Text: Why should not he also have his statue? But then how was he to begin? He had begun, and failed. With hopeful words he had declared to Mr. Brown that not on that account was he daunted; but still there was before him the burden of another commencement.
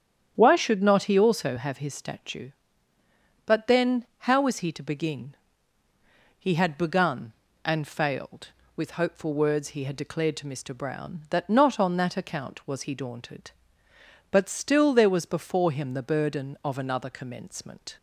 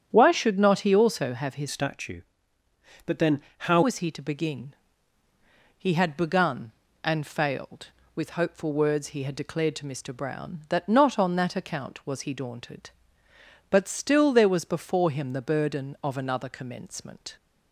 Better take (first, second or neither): first